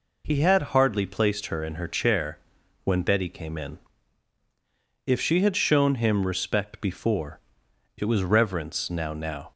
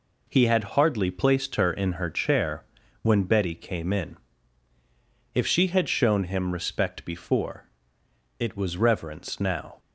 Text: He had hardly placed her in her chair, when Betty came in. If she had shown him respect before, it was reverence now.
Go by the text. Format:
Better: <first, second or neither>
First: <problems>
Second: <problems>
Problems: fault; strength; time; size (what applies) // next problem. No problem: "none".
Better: second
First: says "now" twice; at 9.1 s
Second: none